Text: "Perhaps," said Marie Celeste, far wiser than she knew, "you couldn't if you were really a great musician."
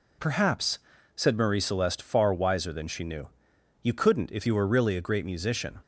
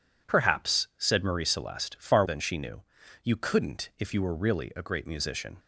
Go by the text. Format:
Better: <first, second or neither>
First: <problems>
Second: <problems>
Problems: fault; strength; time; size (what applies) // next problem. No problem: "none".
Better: first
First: none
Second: skips "wiser"; at 2.2 s